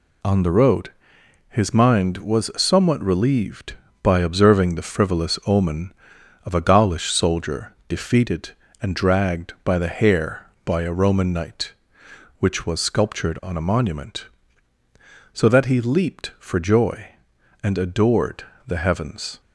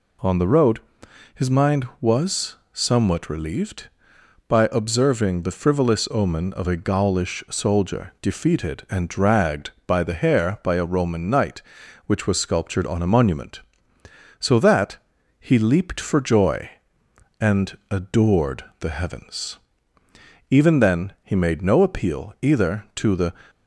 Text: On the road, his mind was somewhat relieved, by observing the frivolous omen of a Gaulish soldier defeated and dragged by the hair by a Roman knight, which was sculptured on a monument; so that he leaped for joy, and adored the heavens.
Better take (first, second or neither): first